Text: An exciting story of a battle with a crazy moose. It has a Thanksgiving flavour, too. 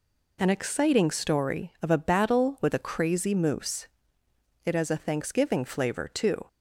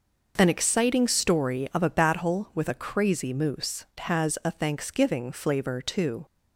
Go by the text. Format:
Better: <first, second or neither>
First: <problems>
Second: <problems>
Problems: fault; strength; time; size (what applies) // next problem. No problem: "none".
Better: first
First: none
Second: skips "It"; at 3.9 s